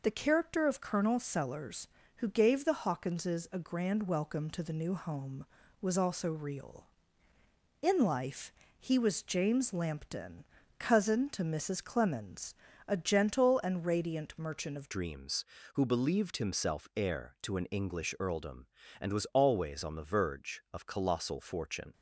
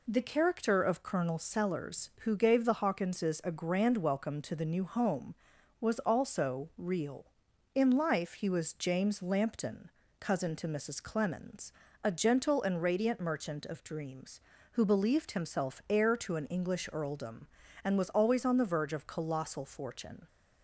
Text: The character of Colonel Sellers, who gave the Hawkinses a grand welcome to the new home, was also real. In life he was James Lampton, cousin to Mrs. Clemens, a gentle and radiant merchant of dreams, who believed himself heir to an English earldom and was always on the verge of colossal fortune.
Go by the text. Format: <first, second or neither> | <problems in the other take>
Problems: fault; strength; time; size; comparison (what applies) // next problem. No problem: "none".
second | pauses between "life" and "he"; slight; at 8.5 s; 0.26 s long // changes voice at "dreams"; from 14.8 s on; 7.1 s long